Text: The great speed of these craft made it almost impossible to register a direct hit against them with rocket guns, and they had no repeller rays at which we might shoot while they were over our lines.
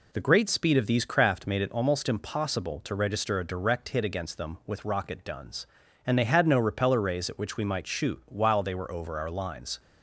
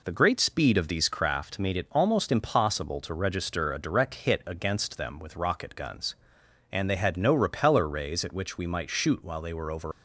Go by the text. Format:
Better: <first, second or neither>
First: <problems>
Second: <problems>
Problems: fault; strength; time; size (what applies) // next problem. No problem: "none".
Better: first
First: none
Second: stops before "our lines"; at 9.9 s